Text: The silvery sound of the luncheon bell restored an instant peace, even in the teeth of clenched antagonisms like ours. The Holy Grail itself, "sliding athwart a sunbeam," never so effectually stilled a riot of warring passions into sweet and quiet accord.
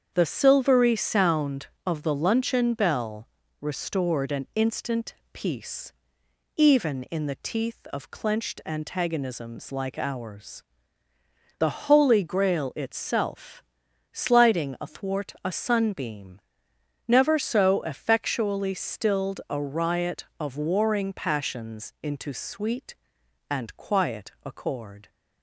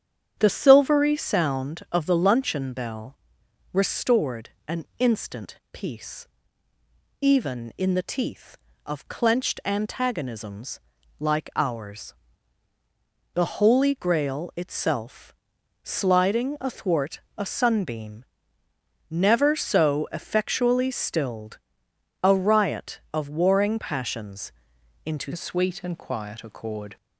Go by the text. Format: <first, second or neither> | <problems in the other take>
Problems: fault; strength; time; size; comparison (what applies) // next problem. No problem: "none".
first | starts louder than the rest; strong; until 1.3 s; 9 dB; strong in the first // pauses between "bell" and "restored"; noticeable; at 3.1 s; 0.56 s long; slight in the first // pauses between "restored" and "an"; slight; at 4.5 s; 0.16 s long // pauses between "instant" and "peace"; slight; at 5.5 s; 0.16 s long; slight in the first // pauses between "antagonisms" and "like"; at 10.7 s; 0.40 s long // pauses between "stilled" and "a"; noticeable; at 21.5 s; 0.66 s long // pauses between "passions" and "into"; noticeable; at 24.5 s; 0.52 s long // changes voice at "sweet"; from 25.3 s on; 1.6 s long